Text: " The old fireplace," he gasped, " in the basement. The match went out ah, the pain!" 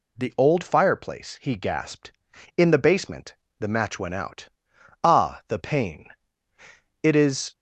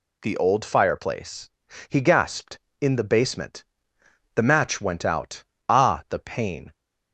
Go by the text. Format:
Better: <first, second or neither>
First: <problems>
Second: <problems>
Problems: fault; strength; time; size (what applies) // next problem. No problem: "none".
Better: second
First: pauses between "out" and "ah"; noticeable; at 4.4 s; 0.56 s long // goes on to say "It is"; from 7.0 s on; 0.52 s long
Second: pauses between "out" and "ah"; slight; at 5.4 s; 0.24 s long